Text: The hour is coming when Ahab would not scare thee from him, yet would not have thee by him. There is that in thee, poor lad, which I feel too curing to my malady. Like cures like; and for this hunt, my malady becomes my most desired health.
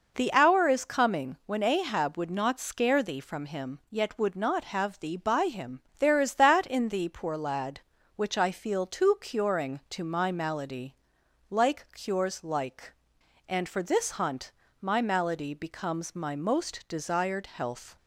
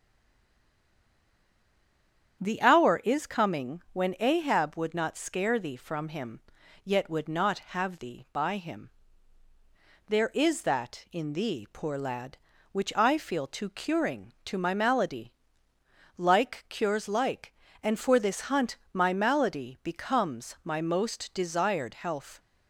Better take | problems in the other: first | stays silent before the first word; until 2.4 s; 2.4 s long // starts louder than the rest; strong; until 3.4 s; 8.5 dB

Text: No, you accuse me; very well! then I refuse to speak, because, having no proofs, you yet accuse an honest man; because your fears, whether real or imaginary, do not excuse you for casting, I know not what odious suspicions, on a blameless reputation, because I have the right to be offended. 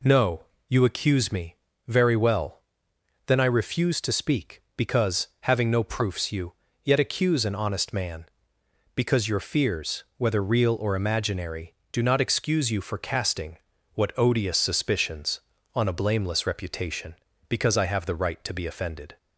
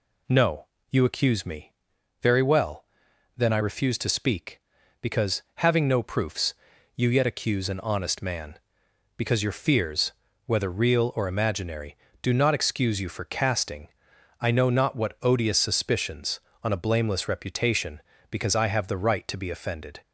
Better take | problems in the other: second | pauses between "you" and "yet"; slight; at 6.5 s; 0.28 s long // skips "I know not"; at 13.7 s

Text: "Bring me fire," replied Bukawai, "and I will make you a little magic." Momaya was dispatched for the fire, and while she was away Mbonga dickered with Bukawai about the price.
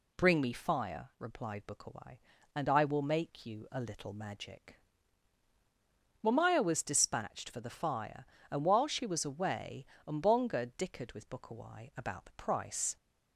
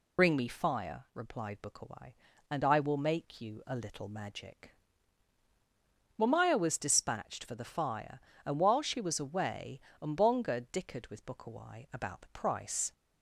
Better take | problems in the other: first | loses the start of "Bring"; at 0.1 s; 80 ms // pauses between "away" and "Mbonga"; slight; at 9.7 s; 0.20 s long; slight in the first

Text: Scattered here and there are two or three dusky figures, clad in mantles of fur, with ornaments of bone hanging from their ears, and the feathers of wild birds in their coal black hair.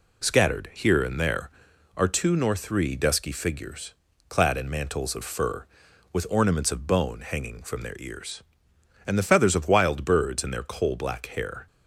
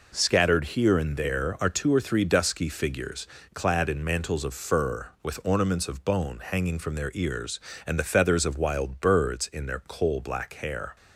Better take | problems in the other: second | says "nor" for "or"; at 2.3 s

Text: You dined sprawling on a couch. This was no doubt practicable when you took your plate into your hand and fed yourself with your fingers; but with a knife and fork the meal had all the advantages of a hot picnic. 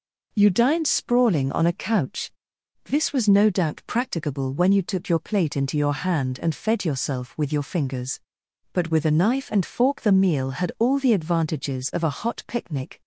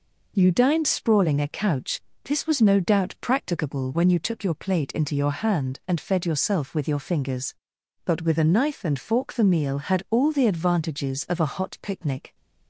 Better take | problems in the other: first | skips "on"; at 1.3 s

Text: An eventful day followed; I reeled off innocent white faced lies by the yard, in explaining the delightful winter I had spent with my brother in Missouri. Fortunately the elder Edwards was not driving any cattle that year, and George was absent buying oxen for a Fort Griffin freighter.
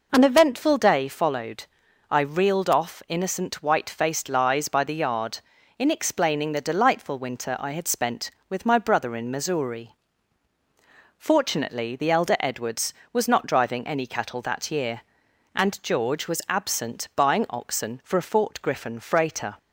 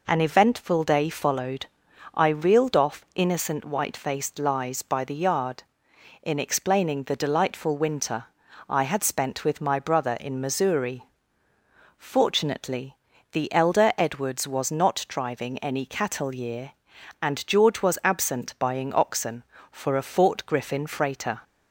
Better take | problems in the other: first | pauses between "winter" and "I"; at 8.2 s; 0.44 s long // pauses between "Fortunately" and "the"; slight; at 12.9 s; 0.36 s long // skips "that"; at 16.3 s

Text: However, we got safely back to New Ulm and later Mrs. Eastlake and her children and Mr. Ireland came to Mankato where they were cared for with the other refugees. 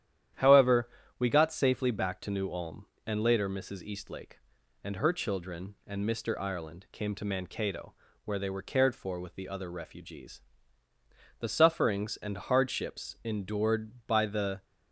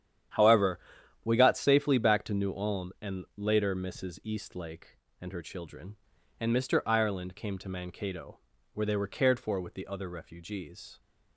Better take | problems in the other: second | starts louder than the rest; strong; until 1.6 s; 10.5 dB; strong in the second // pauses between "Mankato" and "where"; slight; at 7.9 s; 0.32 s long; slight in the second // goes on to say "The sufferings and hardships endured by the"; strong; from 11.3 s on; 3.2 s long

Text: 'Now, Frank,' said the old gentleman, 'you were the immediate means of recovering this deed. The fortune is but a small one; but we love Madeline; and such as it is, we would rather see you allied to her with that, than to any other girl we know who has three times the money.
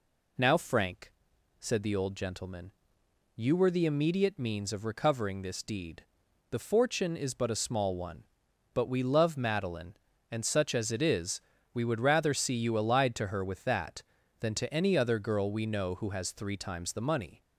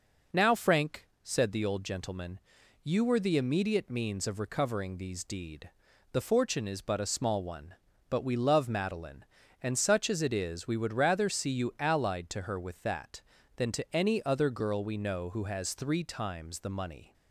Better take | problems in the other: first | says "these" for "this"; at 4.9 s

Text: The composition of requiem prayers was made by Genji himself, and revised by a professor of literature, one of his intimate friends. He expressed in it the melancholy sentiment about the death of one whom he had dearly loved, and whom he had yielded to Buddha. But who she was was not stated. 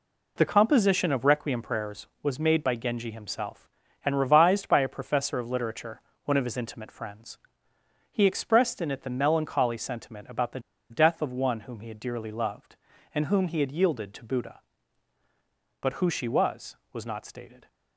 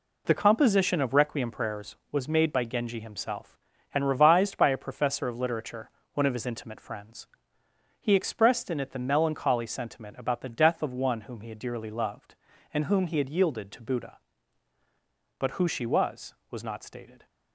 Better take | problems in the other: second | pauses between "the" and "death"; slight; at 10.5 s; 0.31 s long

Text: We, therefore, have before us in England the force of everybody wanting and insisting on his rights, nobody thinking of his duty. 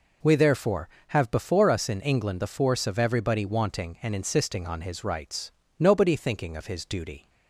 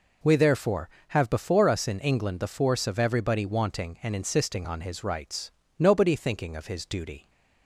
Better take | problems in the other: neither | none

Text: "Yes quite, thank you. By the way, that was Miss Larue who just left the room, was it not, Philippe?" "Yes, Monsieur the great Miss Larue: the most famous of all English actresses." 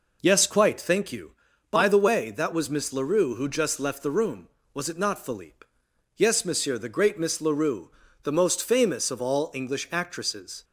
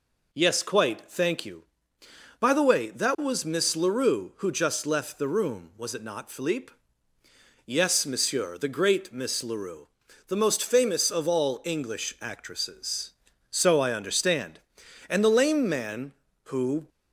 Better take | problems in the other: first | goes on to say "So I understand And the lame man who"; strong; from 13.4 s on; 3.4 s long

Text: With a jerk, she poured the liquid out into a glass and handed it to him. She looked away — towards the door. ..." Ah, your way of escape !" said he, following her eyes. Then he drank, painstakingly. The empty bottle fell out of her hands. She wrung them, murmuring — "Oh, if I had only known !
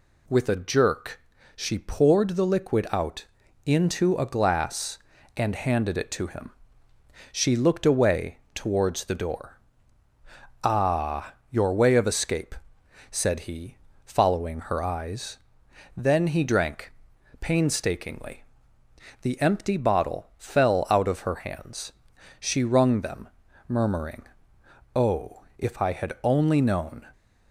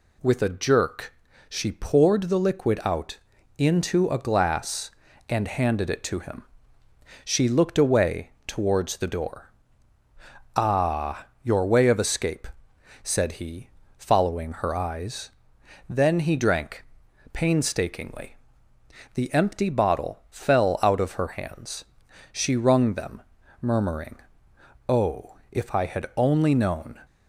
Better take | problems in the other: neither | pauses between "out" and "into"; the same in both

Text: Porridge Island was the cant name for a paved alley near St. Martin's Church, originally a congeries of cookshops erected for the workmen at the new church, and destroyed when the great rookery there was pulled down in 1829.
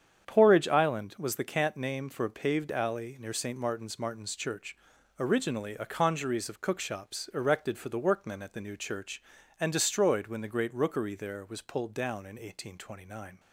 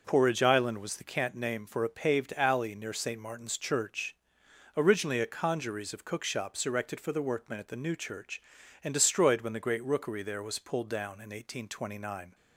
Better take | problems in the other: second | starts louder than the rest; strong; until 1.3 s; 8 dB // says "Martin's" twice; at 3.9 s

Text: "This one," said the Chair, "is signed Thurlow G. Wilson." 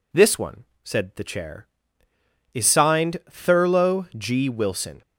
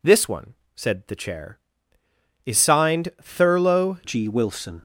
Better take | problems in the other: first | changes voice at "G"; from 4.0 s on; 0.8 s long

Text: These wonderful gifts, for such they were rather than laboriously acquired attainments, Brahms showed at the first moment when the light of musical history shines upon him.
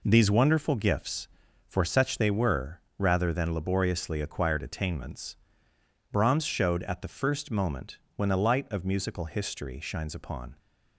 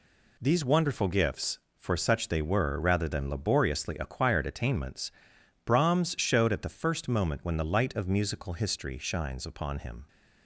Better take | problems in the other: second | pauses between "were" and "rather"; slight; at 2.8 s; 0.16 s long // pauses between "moment" and "when"; slight; at 7.9 s; 0.18 s long // stops before "him"; at 10.5 s

